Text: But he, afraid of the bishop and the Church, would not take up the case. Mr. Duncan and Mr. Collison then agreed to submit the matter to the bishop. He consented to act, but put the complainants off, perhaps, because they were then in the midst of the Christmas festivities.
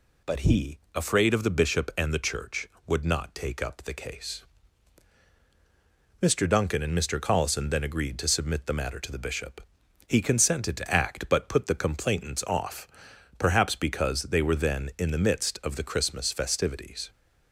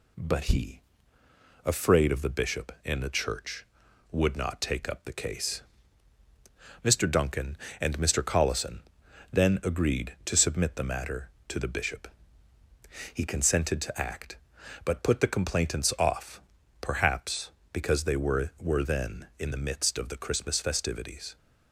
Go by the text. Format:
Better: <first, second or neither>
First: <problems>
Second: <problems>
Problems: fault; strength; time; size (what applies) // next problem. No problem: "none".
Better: first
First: none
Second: pauses between "Collison" and "then"; noticeable; at 8.8 s; 0.52 s long // says "were" twice; at 18.6 s